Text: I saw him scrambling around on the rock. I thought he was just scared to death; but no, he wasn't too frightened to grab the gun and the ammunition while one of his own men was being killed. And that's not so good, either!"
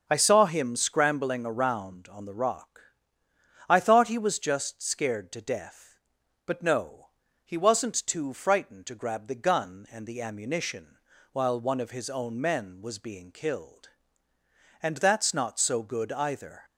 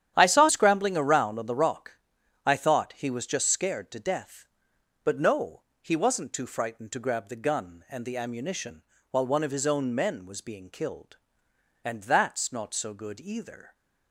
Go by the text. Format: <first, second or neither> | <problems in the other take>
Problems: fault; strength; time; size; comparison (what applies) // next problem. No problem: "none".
first | starts louder than the rest; strong; until 1.1 s; 10.5 dB; also in the first // skips "him"; at 0.4 s // pauses between "ammunition" and "while"; slight; at 8.8 s; 0.26 s long; slight in the first